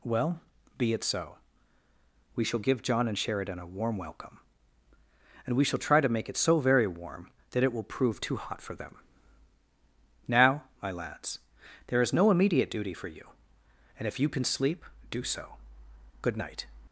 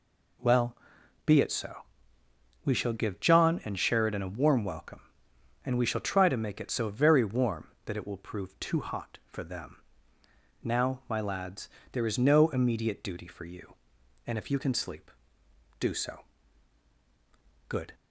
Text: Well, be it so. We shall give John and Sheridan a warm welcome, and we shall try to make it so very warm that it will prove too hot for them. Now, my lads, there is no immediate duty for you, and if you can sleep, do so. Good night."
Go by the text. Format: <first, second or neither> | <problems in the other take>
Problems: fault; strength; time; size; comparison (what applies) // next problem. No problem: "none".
first | stops before "night"; at 17.9 s